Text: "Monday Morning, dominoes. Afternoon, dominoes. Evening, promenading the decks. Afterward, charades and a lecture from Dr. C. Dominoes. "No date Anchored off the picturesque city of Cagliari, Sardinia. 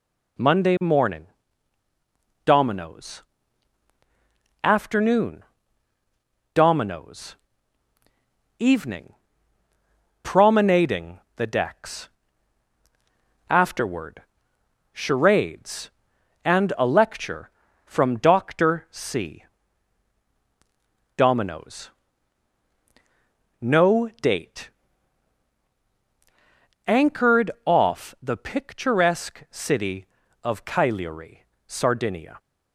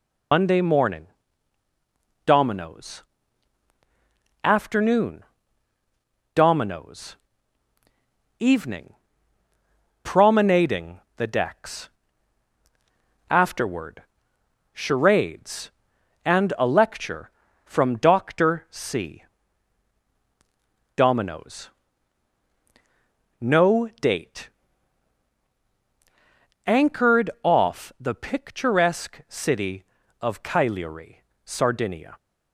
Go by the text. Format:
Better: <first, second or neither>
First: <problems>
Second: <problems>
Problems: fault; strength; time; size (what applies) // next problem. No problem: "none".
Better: first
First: pauses between "promenading" and "the"; slight; at 11.1 s; 0.16 s long // pauses between "date" and "Anchored"; strong; at 24.6 s; 2.1 s long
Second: loses the start of "Monday"; at 0.3 s; 90 ms // pauses between "promenading" and "the"; slight; at 11.0 s; 0.16 s long // pauses between "date" and "Anchored"; strong; at 24.4 s; 2.1 s long